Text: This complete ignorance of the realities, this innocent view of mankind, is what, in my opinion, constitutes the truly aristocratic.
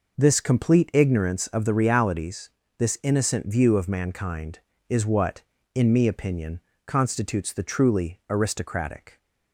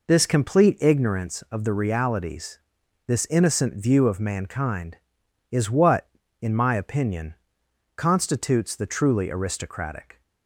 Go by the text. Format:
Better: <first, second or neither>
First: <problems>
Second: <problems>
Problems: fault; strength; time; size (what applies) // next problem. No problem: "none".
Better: second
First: says "me" for "my"; at 5.9 s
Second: none